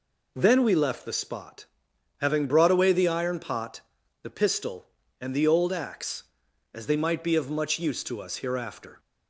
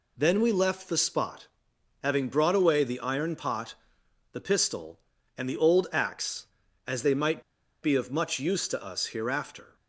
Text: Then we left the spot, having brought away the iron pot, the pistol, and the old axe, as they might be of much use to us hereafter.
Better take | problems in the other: first | pauses between "might" and "be"; at 7.4 s; 0.40 s long

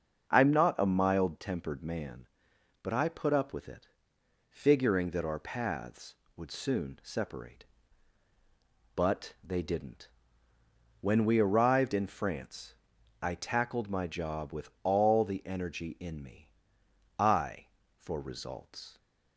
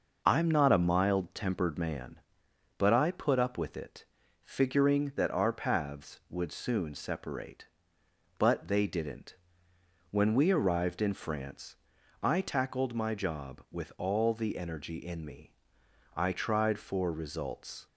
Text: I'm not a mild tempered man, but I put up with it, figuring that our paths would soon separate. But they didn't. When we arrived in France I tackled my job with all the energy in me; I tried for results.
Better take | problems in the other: second | starts louder than the rest; until 1.3 s; 6 dB // pauses between "France" and "I"; noticeable; at 12.7 s; 0.48 s long; noticeable in the second // skips "tried"; at 17.8 s

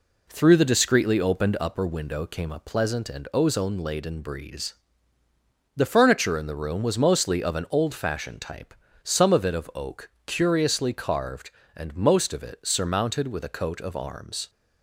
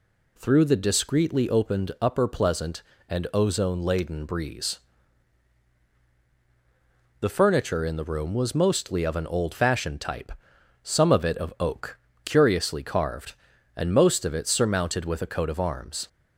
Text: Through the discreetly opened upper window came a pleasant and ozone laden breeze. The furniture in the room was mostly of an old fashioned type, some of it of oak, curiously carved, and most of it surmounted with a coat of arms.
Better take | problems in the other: first | skips "window came a"; at 2.2 s

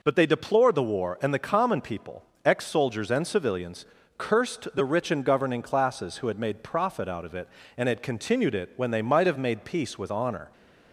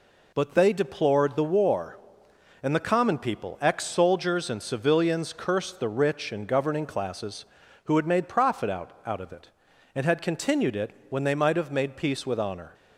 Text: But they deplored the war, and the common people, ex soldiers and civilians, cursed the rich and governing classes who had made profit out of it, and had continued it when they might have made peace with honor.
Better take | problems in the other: first | says "out" twice; at 9.0 s // pauses between "it" and "when"; slight; at 10.9 s; 0.18 s long

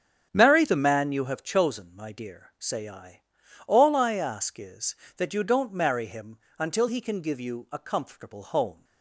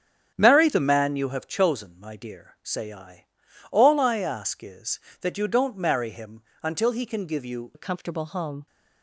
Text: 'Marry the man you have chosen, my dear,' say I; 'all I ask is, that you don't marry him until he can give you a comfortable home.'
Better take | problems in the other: first | starts louder than the rest; strong; until 1.3 s; 7.5 dB; strong in the first // pauses between "him" and "until"; slight; at 6.4 s; 0.22 s long; slight in the first // changes voice at "a"; from 7.7 s on; 0.9 s long

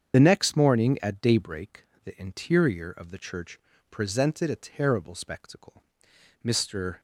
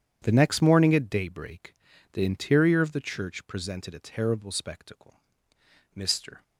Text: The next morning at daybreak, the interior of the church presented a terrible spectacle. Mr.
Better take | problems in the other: second | loses the start of "The"; at 0.1 s; 30 ms // starts louder than the rest; strong; until 1.1 s; 7.5 dB // pauses between "church" and "presented"; slight; at 3.5 s; 0.32 s long

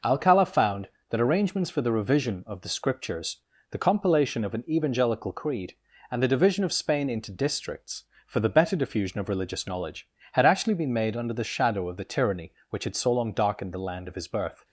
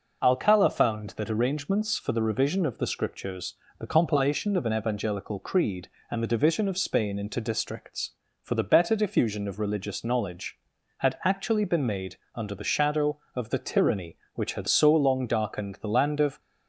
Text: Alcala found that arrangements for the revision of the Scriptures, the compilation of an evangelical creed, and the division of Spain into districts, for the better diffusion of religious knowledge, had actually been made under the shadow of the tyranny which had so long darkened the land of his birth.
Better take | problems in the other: first | pauses between "made" and "under"; slight; at 12.1 s; 0.18 s long // stops before "his birth"; at 16.3 s

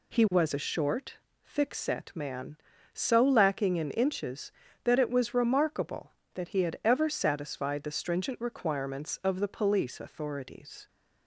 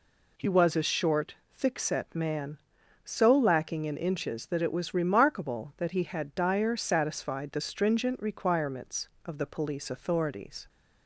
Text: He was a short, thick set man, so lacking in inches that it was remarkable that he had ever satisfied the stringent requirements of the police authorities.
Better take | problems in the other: first | says "dyer" for "ever"; at 6.3 s

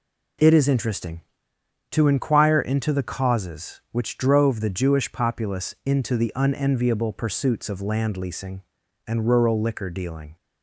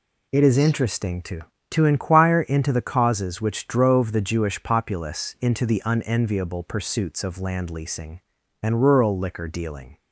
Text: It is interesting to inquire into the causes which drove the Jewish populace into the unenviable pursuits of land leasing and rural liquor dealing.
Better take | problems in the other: first | says "to" twice; at 1.7 s

